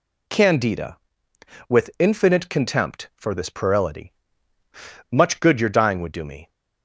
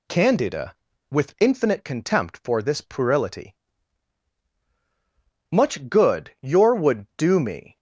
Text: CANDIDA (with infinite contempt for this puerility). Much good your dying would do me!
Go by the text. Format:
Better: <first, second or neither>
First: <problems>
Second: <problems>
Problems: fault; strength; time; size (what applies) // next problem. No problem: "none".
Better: first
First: none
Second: skips "dying"; at 6.7 s